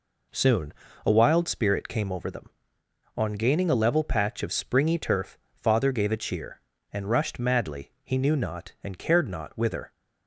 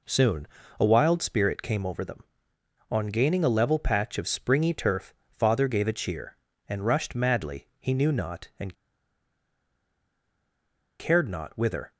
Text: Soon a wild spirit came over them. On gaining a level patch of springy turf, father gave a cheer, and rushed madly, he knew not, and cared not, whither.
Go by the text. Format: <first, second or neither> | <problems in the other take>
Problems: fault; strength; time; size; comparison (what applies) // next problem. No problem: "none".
first | pauses between "Soon" and "a"; slight; at 0.4 s; 0.32 s long; slight in the first // pauses between "and" and "cared"; strong; at 8.7 s; 2.2 s long